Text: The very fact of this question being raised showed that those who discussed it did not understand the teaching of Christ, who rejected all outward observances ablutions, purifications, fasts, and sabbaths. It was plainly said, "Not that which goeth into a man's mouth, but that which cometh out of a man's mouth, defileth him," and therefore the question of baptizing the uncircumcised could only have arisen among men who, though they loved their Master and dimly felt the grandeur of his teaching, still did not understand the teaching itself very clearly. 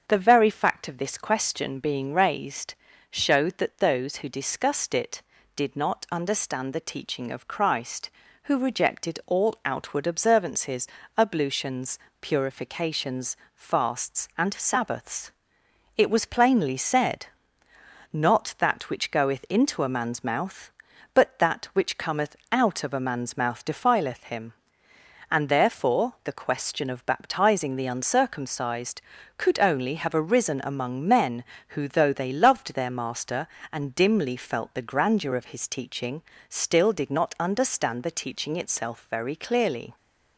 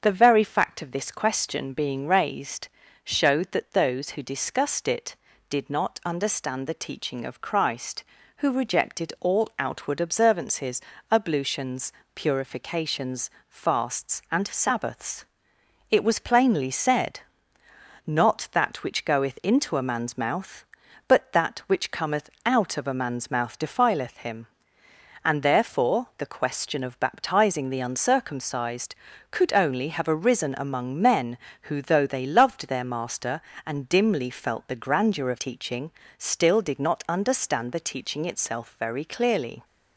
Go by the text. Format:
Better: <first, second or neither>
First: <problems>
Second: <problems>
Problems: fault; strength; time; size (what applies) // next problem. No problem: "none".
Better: first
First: starts louder than the rest; strong; until 1.0 s; 7.5 dB // pauses between "raised" and "showed"; slight; at 2.7 s; 0.36 s long // pauses between "observances" and "ablutions"; slight; at 10.8 s; 0.30 s long // pauses between "cometh" and "out"; slight; at 22.3 s; 0.16 s long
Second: starts louder than the rest; strong; until 1.0 s; 7.5 dB // pauses between "raised" and "showed"; slight; at 2.6 s; 0.36 s long // pauses between "observances" and "ablutions"; slight; at 10.8 s; 0.30 s long // pauses between "cometh" and "out"; slight; at 22.3 s; 0.16 s long // skips "his"; at 35.3 s